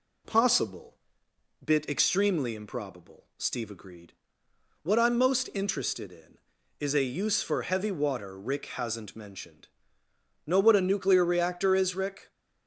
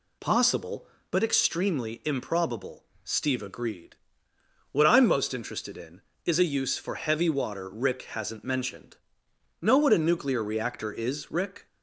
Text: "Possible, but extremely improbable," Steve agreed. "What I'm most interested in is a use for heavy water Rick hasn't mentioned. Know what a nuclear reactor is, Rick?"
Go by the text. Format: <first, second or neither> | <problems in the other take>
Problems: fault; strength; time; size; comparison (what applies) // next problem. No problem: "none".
second | says "bit" for "but"; at 1.6 s